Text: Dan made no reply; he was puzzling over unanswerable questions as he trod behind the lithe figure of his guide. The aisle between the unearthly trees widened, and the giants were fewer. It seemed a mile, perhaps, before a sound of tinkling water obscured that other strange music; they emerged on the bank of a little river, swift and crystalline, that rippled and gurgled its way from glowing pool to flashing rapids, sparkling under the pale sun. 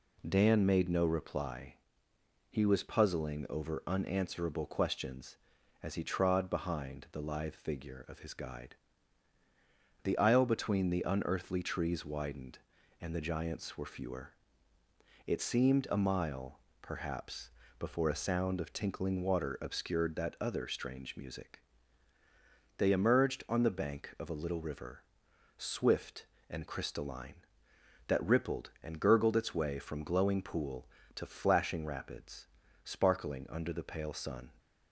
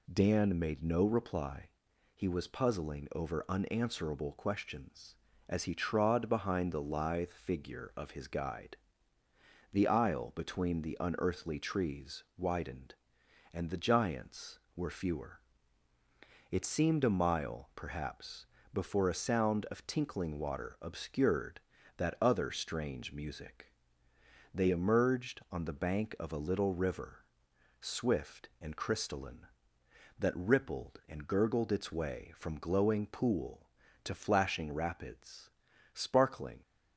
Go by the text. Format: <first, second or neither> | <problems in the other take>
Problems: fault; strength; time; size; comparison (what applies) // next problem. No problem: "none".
first | stops before "under the pale sun"; at 36.6 s